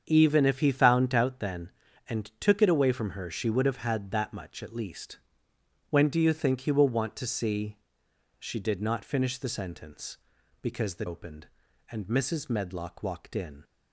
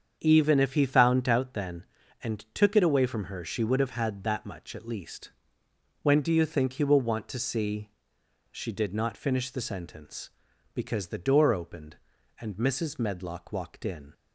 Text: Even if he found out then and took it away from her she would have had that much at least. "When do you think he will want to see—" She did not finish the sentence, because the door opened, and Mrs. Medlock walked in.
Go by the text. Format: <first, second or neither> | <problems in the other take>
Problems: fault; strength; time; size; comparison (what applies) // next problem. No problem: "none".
second | starts louder than the rest; strong; until 1.0 s; 7.5 dB; strong in the second // skips "door"; at 11.0 s